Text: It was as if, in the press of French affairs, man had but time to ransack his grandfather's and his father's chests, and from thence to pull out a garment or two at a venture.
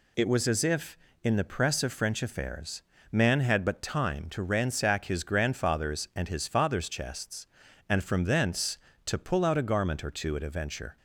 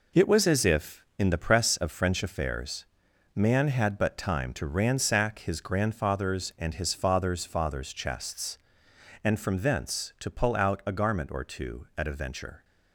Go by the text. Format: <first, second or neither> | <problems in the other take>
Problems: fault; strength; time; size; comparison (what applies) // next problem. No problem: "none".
first | says "father's" twice; at 7.4 s